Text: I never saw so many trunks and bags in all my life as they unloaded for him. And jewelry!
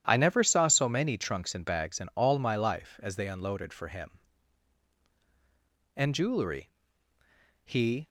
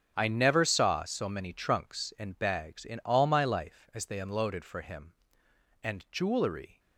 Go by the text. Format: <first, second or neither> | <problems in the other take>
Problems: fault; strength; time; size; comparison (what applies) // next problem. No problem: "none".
second | starts louder than the rest; strong; until 1.0 s; 10.5 dB; strong in the second // goes on to say "He"; slight; from 7.6 s on; 0.44 s long